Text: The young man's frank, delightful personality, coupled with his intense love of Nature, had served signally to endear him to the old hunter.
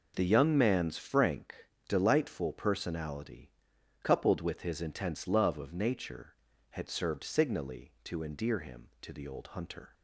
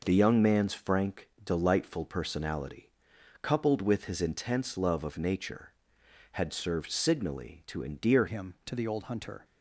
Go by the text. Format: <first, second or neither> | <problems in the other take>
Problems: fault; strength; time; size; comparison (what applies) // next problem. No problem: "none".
first | changes voice at "him"; from 8.2 s on; 1.2 s long